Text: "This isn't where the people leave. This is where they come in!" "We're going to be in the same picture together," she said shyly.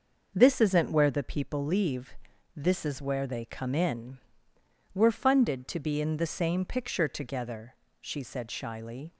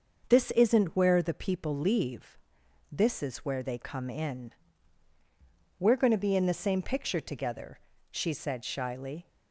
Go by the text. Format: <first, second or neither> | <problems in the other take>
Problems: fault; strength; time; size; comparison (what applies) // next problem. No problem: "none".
second | starts louder than the rest; until 1.3 s; 6 dB; also in the second // says "funded" for "going"; at 5.1 s